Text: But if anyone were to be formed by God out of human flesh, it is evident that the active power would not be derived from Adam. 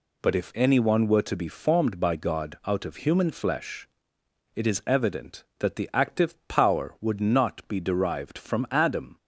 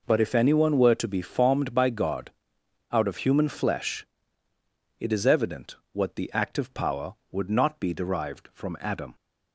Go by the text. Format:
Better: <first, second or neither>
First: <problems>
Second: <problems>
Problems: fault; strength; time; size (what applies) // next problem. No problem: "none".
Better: first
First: none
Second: pauses between "God" and "out"; noticeable; at 2.3 s; 0.60 s long // says "what" for "that"; at 5.9 s